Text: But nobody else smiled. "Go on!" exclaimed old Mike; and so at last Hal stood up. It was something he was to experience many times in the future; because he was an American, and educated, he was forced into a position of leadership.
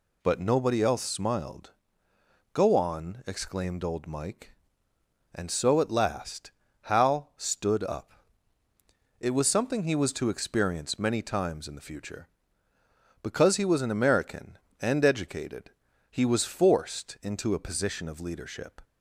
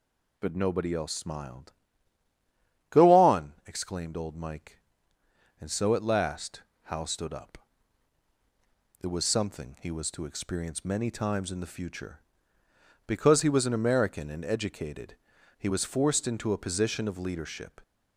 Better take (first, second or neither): neither